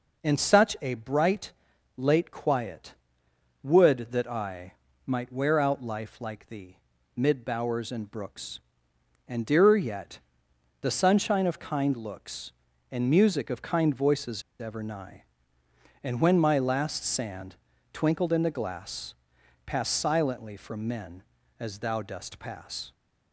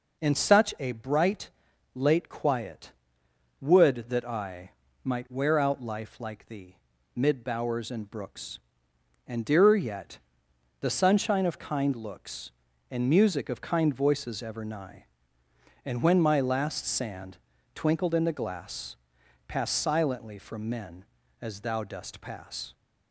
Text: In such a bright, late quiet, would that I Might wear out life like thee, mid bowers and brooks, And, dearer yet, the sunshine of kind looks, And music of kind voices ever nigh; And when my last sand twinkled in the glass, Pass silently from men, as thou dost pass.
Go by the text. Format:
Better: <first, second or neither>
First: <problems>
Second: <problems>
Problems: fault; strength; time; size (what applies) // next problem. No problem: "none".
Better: second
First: pauses between "I" and "Might"; slight; at 4.7 s; 0.32 s long // pauses between "voices" and "ever"; slight; at 14.4 s; 0.17 s long // pauses between "sand" and "twinkled"; slight; at 17.5 s; 0.36 s long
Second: pauses between "I" and "Might"; slight; at 4.7 s; 0.32 s long // pauses between "sand" and "twinkled"; slight; at 17.3 s; 0.36 s long